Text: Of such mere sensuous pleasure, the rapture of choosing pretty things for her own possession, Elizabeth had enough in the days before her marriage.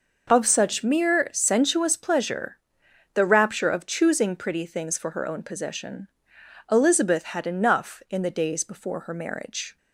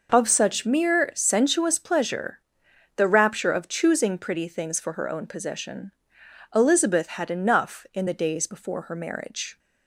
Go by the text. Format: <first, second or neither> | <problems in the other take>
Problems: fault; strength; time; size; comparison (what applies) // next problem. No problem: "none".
neither | none